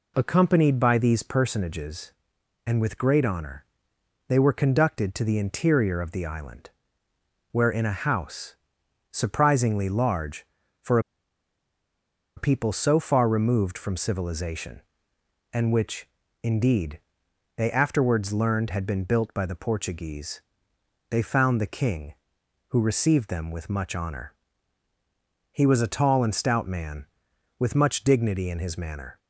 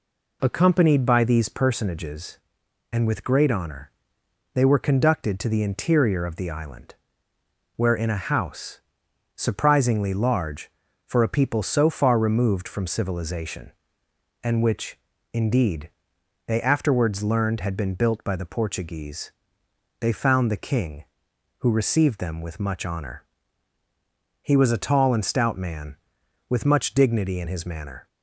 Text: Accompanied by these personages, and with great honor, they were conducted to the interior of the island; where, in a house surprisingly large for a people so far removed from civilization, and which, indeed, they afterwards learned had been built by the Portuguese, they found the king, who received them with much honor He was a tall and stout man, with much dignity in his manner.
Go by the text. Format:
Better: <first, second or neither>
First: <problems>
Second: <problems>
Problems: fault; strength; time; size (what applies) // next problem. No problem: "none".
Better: second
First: pauses between "house" and "surprisingly"; noticeable; at 8.5 s; 0.56 s long // pauses between "for" and "a"; strong; at 10.9 s; 1.3 s long // pauses between "honor" and "He"; at 24.3 s; 1.1 s long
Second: pauses between "house" and "surprisingly"; noticeable; at 8.7 s; 0.56 s long // pauses between "honor" and "He"; at 23.2 s; 1.1 s long